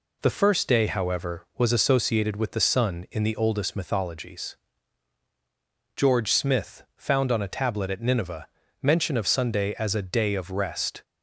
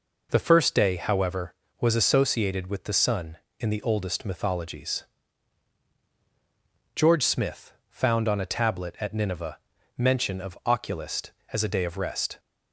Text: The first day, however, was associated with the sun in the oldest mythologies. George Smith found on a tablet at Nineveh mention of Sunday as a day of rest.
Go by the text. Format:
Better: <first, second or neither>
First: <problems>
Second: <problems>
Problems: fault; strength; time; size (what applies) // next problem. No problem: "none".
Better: first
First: pauses between "Nineveh" and "mention"; slight; at 8.4 s; 0.34 s long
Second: pauses between "Smith" and "found"; slight; at 7.7 s; 0.16 s long // pauses between "Nineveh" and "mention"; at 9.5 s; 0.40 s long // says "Oculist" for "Sunday"; at 10.6 s